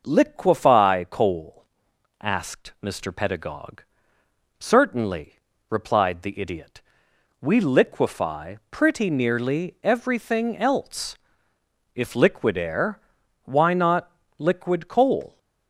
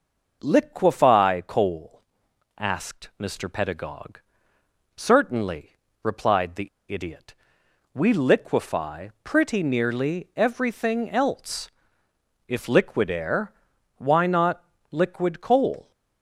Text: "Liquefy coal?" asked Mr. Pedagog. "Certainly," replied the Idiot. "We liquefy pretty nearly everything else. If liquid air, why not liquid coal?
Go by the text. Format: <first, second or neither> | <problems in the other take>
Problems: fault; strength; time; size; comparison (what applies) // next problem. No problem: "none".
first | pauses between "the" and "Idiot"; slight; at 6.6 s; 0.21 s long // pauses between "not" and "liquid"; slight; at 14.6 s; 0.28 s long; slight in the first